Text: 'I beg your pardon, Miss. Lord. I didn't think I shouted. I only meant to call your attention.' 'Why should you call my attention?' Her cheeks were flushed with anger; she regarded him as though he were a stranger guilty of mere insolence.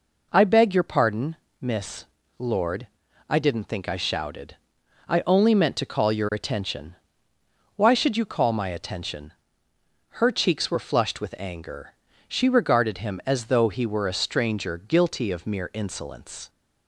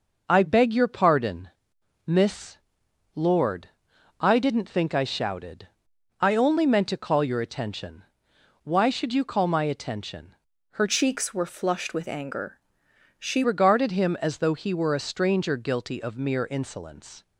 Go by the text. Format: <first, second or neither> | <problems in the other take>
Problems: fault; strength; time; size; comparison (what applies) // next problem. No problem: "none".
first | changes voice from "cheeks" to "she"; from 10.8 to 13.4 s; 2.6 s long